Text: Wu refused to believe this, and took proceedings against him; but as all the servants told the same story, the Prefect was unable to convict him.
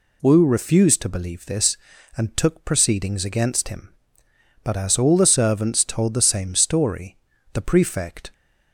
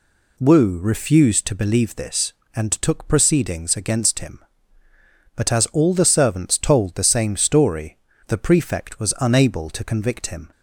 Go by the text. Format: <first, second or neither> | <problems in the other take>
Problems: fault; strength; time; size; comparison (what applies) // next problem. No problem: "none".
second | stops before "was unable to convict him"; at 8.3 s